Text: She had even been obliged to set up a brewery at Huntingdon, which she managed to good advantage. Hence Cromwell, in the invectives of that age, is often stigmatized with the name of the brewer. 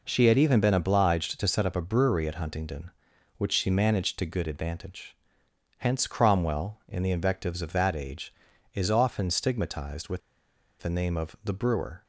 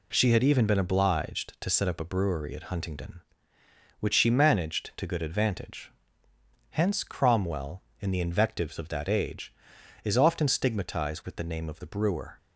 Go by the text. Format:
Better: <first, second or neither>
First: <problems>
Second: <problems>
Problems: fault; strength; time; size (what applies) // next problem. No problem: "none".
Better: second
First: pauses between "with" and "the"; noticeable; at 10.2 s; 0.61 s long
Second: none